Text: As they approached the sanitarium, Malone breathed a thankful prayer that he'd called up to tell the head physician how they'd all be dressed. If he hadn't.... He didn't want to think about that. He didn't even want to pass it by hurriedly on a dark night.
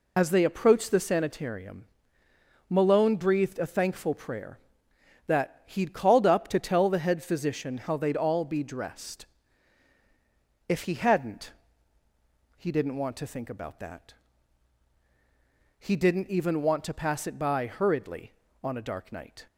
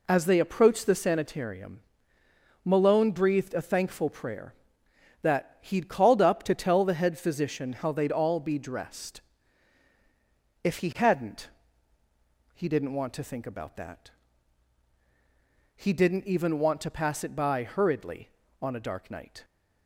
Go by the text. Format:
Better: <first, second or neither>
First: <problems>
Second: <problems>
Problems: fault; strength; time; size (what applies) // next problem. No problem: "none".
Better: second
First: loses the start of "As"; at 0.1 s; 50 ms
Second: none